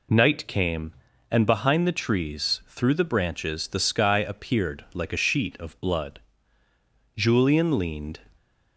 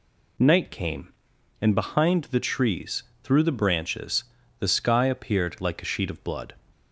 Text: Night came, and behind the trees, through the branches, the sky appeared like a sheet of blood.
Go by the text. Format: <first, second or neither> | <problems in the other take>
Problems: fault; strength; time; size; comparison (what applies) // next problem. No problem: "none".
second | goes on to say "Julian leaned"; noticeable; from 7.1 s on; 1.0 s long